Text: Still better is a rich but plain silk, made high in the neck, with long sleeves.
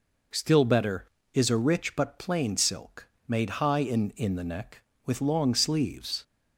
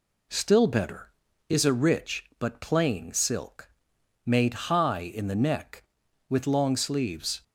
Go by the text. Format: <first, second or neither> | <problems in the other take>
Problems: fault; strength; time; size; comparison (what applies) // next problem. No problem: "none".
second | says "in" twice; at 4.1 s